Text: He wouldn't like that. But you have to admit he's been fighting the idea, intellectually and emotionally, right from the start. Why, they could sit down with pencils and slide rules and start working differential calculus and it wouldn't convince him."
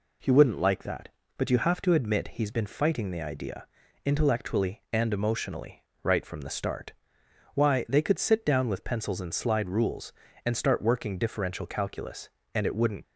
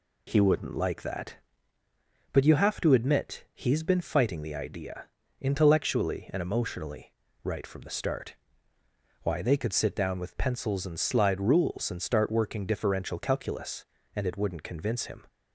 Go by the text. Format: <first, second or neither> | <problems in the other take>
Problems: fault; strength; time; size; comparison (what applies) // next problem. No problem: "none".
second | stops before "convince him"; at 13.0 s